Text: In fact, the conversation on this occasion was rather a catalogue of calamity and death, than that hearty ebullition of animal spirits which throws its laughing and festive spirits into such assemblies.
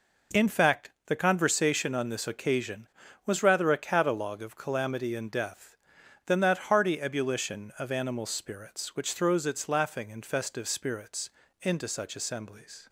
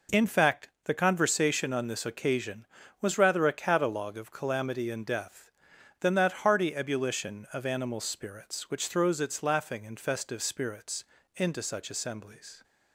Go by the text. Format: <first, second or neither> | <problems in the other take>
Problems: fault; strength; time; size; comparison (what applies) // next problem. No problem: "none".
neither | pauses between "spirits" and "into"; slight; the same in both